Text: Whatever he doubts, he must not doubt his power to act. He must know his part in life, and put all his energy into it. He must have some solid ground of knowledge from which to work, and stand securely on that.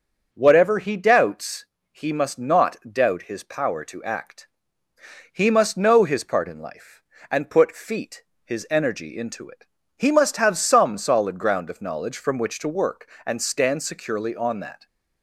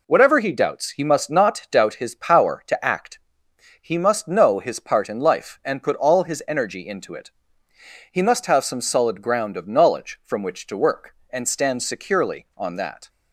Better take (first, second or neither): second